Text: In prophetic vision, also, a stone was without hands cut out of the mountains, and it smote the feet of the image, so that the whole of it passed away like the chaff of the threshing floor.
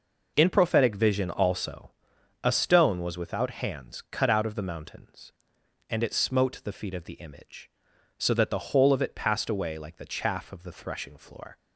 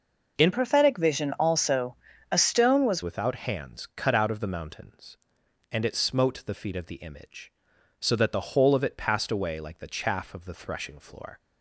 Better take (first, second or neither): first